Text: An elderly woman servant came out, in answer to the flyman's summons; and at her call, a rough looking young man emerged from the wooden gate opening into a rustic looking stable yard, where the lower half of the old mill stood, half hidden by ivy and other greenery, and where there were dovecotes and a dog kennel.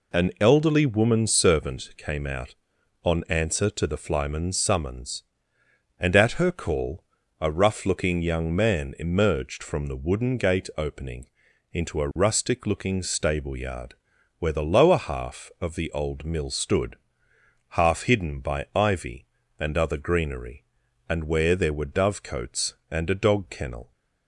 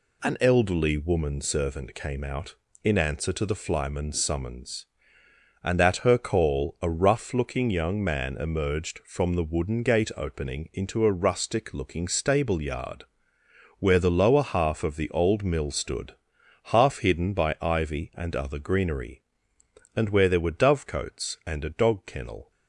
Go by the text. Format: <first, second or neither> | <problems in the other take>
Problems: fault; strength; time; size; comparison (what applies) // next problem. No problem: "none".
second | says "on" for "in"; at 3.0 s // pauses between "opening" and "into"; at 11.2 s; 0.42 s long